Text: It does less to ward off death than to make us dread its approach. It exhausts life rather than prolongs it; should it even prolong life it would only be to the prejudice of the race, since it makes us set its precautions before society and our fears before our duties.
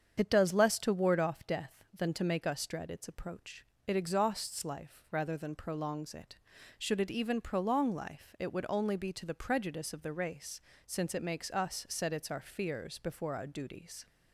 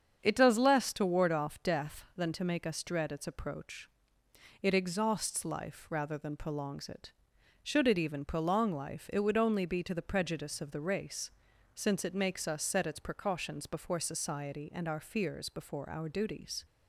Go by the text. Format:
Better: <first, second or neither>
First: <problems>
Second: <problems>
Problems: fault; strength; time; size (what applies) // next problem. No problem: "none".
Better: second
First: starts louder than the rest; strong; until 1.1 s; 7.5 dB // skips "precautions before society and"; at 12.3 s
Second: starts louder than the rest; strong; until 1.2 s; 7.5 dB